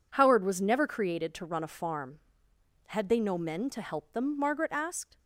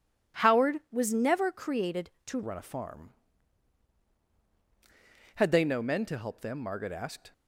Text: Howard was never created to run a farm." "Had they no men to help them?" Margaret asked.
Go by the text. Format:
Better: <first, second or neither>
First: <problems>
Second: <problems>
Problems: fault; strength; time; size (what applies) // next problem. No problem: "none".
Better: first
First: none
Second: changes voice at "run"; from 2.4 s on; 4.9 s long